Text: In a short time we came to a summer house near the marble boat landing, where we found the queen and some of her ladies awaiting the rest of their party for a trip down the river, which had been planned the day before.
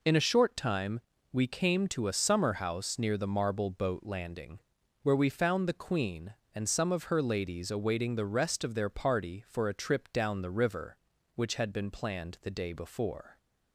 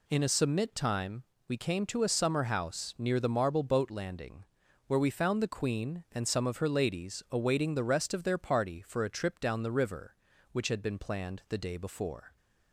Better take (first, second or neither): first